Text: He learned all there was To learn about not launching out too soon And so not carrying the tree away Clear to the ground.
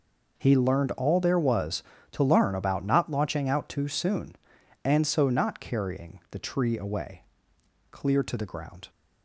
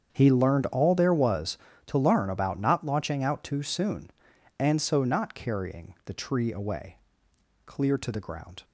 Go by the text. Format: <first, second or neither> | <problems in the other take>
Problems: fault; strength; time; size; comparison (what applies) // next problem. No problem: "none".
first | starts louder than the rest; strong; until 1.3 s; 7.5 dB // pauses between "away" and "Clear"; noticeable; at 6.9 s; 0.70 s long; noticeable in the first